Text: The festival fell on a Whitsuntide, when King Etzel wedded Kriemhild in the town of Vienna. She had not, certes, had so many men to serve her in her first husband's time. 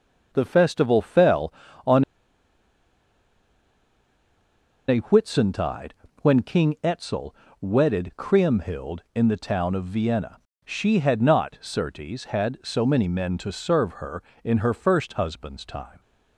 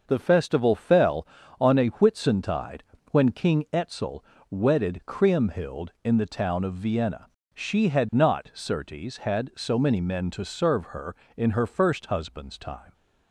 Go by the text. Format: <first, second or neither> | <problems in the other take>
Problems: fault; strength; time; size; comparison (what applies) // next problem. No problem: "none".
second | starts louder than the rest; noticeable; until 1.3 s; 6 dB; noticeable in the second // pauses between "on" and "a"; strong; at 2.0 s; 2.8 s long // pauses between "Etzel" and "wedded"; slight; at 7.3 s; 0.28 s long; slight in the second